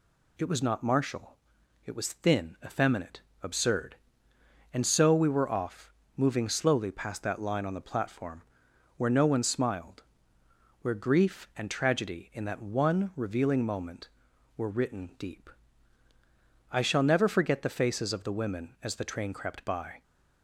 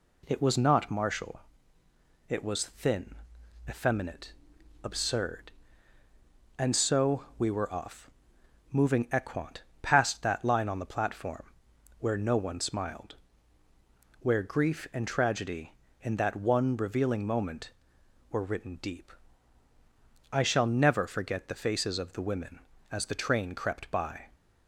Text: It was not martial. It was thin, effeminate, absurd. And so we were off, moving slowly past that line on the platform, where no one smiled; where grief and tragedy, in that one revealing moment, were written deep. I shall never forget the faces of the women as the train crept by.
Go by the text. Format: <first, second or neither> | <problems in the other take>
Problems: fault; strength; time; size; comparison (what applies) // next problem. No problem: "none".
first | says "equant" for "slowly"; at 9.0 s